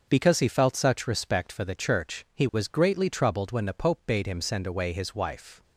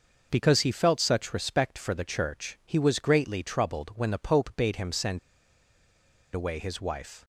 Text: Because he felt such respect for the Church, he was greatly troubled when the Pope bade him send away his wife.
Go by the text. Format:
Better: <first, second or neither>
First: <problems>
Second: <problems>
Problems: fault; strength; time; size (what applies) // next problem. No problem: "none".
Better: first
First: none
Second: starts louder than the rest; noticeable; until 1.3 s; 6 dB // pauses between "send" and "away"; at 5.1 s; 1.1 s long